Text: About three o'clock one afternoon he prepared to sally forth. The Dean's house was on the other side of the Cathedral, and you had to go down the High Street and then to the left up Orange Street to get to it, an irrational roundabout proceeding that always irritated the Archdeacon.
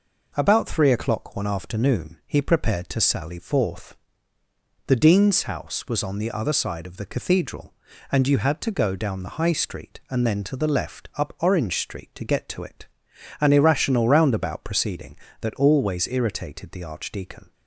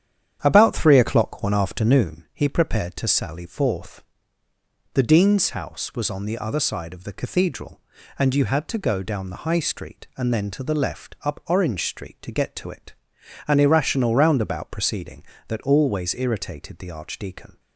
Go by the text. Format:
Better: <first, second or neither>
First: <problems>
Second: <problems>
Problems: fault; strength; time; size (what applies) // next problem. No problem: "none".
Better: first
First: none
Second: starts louder than the rest; strong; until 2.1 s; 9 dB